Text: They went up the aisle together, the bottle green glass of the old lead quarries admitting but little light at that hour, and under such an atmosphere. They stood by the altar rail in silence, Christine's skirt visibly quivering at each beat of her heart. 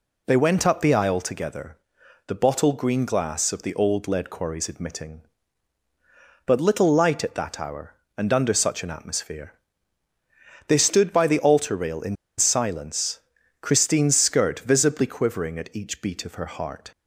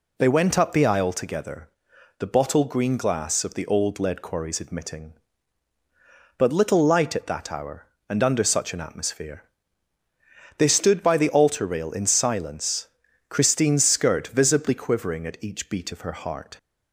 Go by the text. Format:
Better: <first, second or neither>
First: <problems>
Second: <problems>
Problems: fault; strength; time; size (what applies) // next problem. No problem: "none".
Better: second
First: pauses between "in" and "silence"; slight; at 12.1 s; 0.22 s long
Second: none